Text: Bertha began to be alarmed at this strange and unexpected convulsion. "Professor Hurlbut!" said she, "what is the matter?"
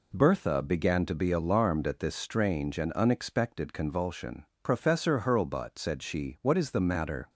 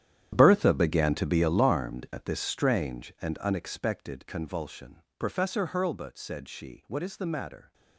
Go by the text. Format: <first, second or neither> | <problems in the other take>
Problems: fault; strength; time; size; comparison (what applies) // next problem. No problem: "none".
first | gets quieter; strong; throughout; 14.5 dB